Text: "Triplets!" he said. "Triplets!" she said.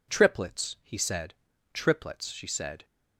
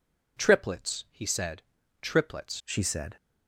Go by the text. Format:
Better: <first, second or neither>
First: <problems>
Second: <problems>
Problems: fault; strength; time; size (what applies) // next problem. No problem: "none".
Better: first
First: none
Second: changes voice at "she"; from 2.6 s on; 0.5 s long